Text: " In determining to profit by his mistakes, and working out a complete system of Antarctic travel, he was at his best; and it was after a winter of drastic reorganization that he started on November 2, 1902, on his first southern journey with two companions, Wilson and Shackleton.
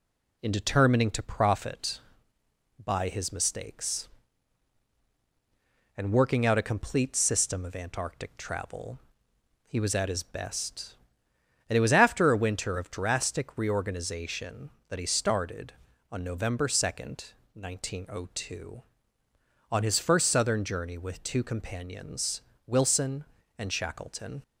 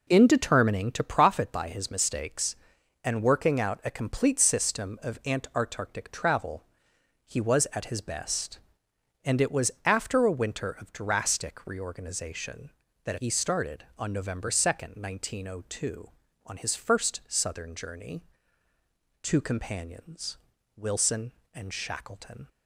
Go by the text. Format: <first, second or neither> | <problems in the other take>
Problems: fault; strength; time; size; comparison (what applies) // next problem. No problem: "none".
first | skips "with"; at 18.7 s